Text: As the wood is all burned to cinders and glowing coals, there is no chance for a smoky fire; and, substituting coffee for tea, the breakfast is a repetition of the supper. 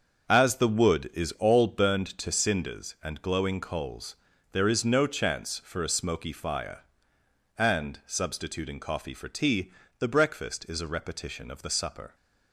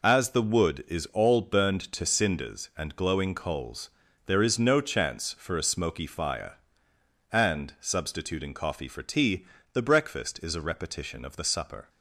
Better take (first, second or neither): second